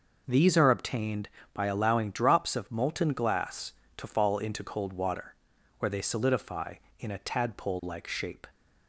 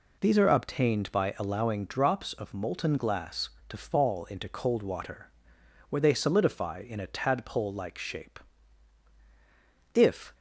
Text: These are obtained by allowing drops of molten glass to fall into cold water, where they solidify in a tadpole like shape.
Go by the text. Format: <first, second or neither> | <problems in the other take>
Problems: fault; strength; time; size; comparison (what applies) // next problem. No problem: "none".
first | goes on to say "If"; slight; from 9.9 s on; 0.40 s long